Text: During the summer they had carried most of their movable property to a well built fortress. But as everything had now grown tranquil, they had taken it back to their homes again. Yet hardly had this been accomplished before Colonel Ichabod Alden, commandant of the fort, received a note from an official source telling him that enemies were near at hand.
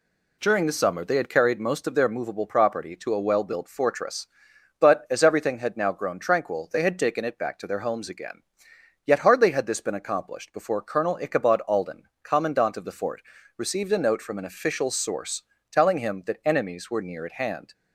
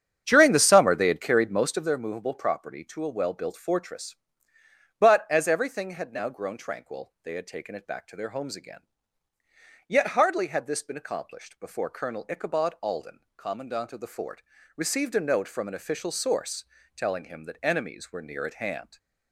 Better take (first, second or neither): first